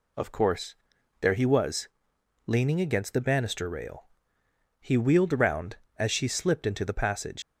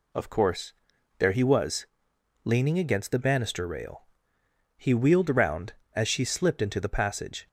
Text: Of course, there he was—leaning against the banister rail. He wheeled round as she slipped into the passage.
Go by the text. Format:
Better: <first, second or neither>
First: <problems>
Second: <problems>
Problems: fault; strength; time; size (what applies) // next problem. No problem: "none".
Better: second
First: leaves "passage" unfinished; at 7.4 s; 95 ms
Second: none